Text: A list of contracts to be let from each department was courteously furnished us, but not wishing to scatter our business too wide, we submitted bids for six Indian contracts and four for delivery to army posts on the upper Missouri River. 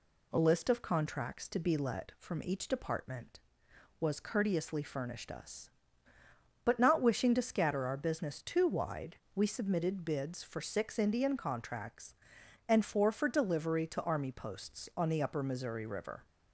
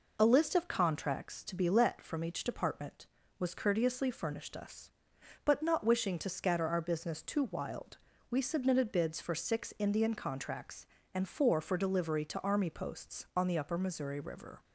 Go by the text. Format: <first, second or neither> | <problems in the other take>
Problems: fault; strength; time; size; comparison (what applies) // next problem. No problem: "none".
first | says "wild" for "wide"; at 7.4 s